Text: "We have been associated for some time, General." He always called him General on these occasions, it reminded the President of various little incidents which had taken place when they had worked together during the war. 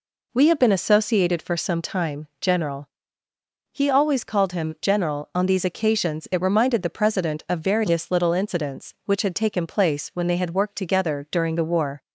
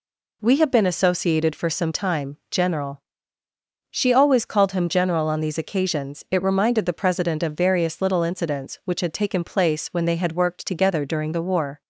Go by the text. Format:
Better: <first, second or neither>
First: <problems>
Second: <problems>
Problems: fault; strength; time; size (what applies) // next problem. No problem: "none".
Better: first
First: none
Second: says "She" for "He"; at 3.9 s